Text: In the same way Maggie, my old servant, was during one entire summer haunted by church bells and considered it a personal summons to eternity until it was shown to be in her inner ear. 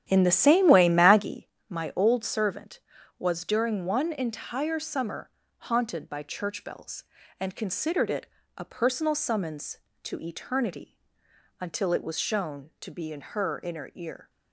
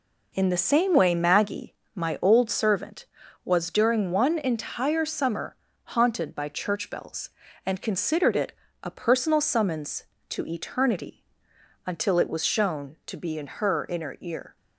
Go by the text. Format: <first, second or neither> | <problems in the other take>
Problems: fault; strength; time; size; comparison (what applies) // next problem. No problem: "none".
second | starts louder than the rest; strong; until 1.4 s; 10.5 dB // pauses between "summer" and "haunted"; slight; at 5.2 s; 0.30 s long; slight in the second // pauses between "it" and "a"; slight; at 8.2 s; 0.30 s long; slight in the second // pauses between "eternity" and "until"; noticeable; at 10.9 s; 0.62 s long; noticeable in the second